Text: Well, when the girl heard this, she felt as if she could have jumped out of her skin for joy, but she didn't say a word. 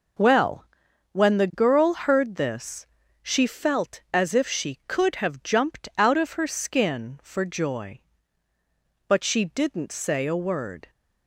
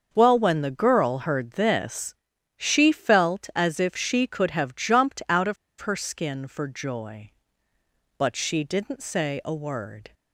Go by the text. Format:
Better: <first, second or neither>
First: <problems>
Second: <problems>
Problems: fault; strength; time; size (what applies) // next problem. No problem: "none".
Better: first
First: none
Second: starts louder than the rest; until 1.1 s; 6.5 dB // pauses between "of" and "her"; slight; at 5.5 s; 0.25 s long